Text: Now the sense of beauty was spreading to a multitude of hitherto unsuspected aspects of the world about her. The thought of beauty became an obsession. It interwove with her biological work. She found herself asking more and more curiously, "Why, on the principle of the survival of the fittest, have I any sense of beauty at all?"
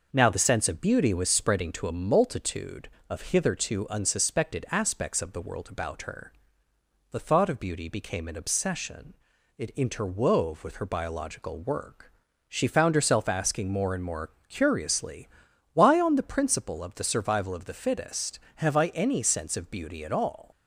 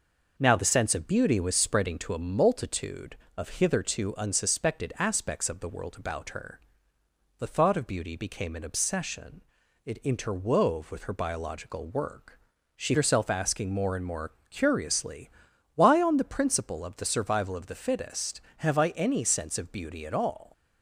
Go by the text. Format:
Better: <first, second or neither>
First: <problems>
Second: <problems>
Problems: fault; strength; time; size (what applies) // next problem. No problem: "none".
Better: first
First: pauses between "more" and "curiously"; slight; at 14.3 s; 0.16 s long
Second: skips "found"; at 12.9 s // pauses between "more" and "curiously"; slight; at 14.3 s; 0.16 s long